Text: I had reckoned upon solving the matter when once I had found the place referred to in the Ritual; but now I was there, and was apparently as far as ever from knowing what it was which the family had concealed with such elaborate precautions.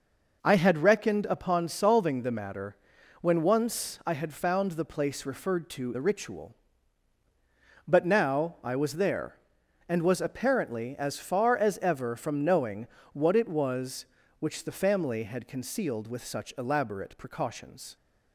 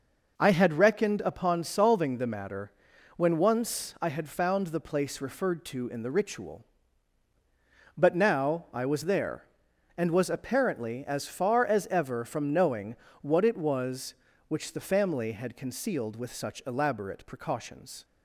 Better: second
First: pauses between "matter" and "when"; at 2.7 s; 0.44 s long // skips "in"; at 5.9 s // pauses between "knowing" and "what"; slight; at 12.8 s; 0.24 s long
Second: pauses between "matter" and "when"; at 2.7 s; 0.44 s long // pauses between "knowing" and "what"; slight; at 12.9 s; 0.24 s long

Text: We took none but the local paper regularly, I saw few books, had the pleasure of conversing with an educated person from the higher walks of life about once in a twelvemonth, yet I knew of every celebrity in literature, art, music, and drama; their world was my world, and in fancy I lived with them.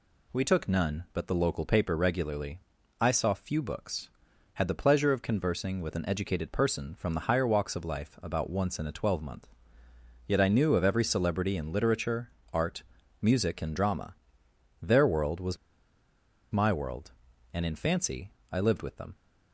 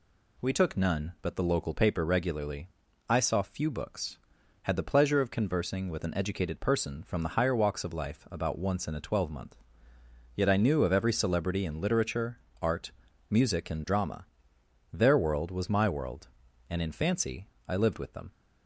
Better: second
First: pauses between "was" and "my"; noticeable; at 15.5 s; 0.95 s long // pauses between "fancy" and "I"; slight; at 18.3 s; 0.18 s long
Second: pauses between "fancy" and "I"; slight; at 17.4 s; 0.18 s long

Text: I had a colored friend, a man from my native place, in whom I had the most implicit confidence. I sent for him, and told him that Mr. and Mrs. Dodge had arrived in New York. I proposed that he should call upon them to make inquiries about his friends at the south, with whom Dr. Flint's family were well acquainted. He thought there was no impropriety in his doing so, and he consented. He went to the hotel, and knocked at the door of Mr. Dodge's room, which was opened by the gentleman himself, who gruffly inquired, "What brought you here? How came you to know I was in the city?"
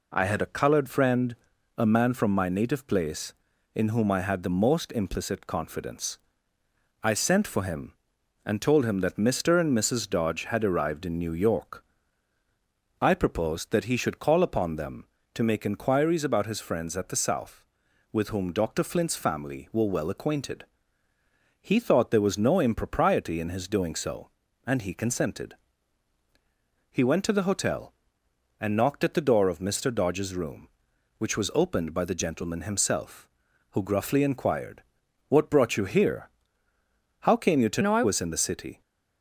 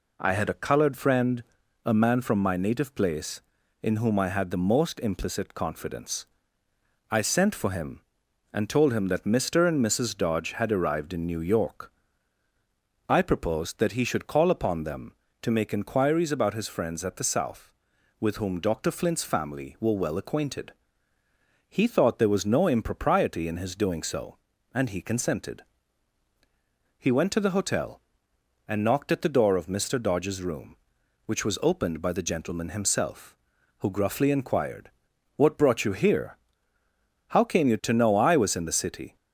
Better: second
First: changes voice from "know" to "I"; from 37.8 to 38.0 s; 0.2 s long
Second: none

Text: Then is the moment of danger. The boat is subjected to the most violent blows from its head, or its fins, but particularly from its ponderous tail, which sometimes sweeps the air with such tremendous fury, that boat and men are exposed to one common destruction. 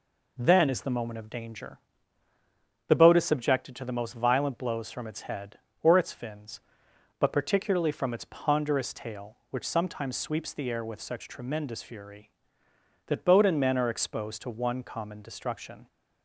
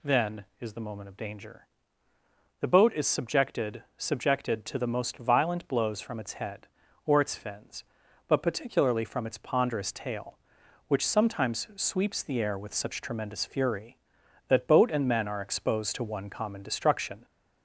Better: first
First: none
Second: says "subjected" twice; at 3.9 s

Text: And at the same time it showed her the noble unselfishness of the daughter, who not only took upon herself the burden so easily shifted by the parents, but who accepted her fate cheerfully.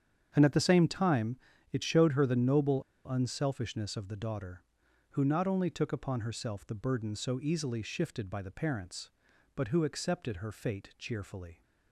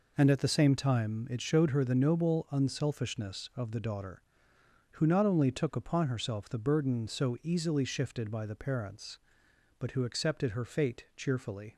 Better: second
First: starts louder than the rest; strong; until 1.3 s; 8 dB // pauses between "time" and "it"; slight; at 1.3 s; 0.34 s long // pauses between "noble" and "unselfishness"; slight; at 2.8 s; 0.25 s long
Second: none

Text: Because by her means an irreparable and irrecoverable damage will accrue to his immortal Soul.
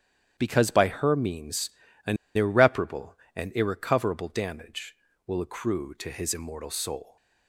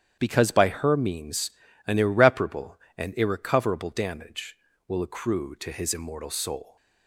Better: second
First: starts louder than the rest; strong; until 1.3 s; 10 dB // pauses between "means" and "an"; slight; at 1.6 s; 0.36 s long // pauses between "an" and "irreparable"; slight; at 2.1 s; 0.19 s long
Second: starts louder than the rest; strong; until 1.2 s; 10 dB // pauses between "means" and "an"; slight; at 1.4 s; 0.36 s long

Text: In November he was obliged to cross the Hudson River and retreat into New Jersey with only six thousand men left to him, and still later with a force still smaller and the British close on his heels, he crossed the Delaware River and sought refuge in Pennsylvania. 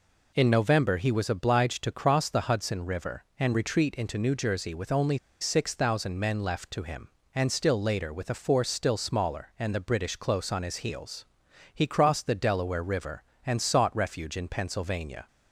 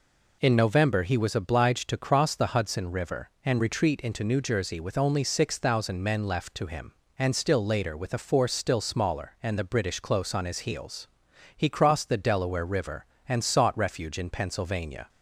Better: second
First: pauses between "only" and "six"; slight; at 5.1 s; 0.22 s long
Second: none

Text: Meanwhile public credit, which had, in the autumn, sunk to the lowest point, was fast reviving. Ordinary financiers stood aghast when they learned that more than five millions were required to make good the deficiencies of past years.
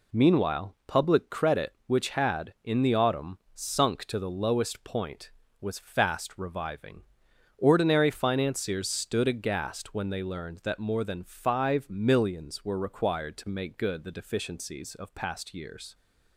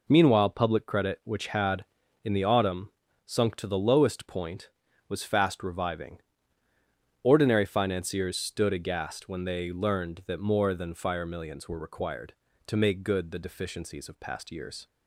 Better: first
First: none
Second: says "fire" for "five"; at 10.9 s

